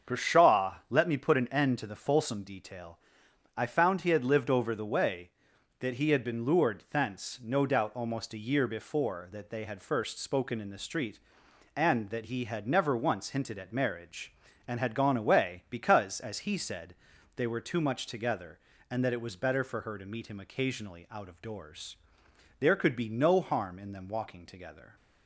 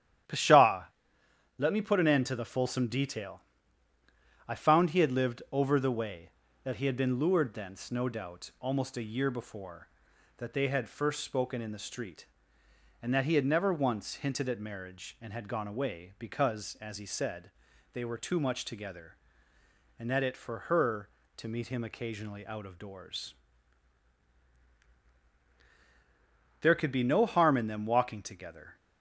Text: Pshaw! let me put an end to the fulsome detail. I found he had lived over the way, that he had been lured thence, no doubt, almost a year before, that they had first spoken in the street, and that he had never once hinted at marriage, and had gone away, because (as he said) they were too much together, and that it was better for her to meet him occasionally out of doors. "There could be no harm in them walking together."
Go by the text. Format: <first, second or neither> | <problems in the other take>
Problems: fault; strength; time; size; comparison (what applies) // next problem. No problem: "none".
first | starts louder than the rest; strong; until 2.0 s; 11 dB; also in the first // skips "was better"; at 20.3 s